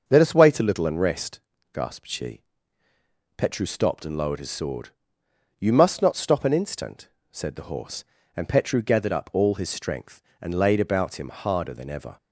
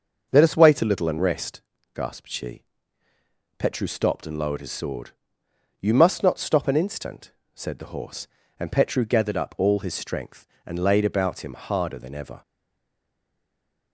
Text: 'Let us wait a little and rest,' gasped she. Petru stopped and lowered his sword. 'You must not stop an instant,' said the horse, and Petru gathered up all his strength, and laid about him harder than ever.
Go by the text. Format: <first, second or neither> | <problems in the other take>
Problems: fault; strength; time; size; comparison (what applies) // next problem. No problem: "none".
first | starts louder than the rest; noticeable; until 1.3 s; 6 dB; noticeable in the first // stays silent after the last word; noticeable; from 12.4 s on; 1.5 s long